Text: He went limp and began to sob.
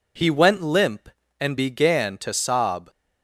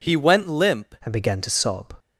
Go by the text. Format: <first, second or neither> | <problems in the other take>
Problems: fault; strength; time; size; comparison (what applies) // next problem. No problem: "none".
first | changes voice at "and"; from 1.0 s on; 0.9 s long